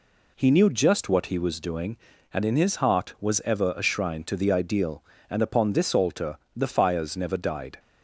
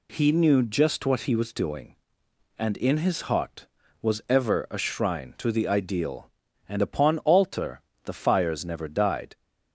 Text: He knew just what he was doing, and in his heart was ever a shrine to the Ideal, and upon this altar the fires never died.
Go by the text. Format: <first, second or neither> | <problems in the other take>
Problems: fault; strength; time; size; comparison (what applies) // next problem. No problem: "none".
first | skips "this"; at 7.1 s // pauses between "altar" and "the"; slight; at 7.8 s; 0.22 s long; slight in the first